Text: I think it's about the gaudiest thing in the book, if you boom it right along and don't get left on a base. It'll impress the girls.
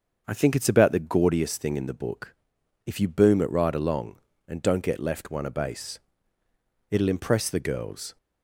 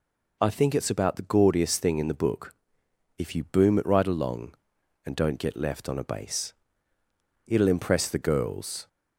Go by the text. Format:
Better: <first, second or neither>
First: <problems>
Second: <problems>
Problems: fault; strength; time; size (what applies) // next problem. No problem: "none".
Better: second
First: starts louder than the rest; until 1.2 s; 6.5 dB // says "one" for "on"; at 5.3 s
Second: none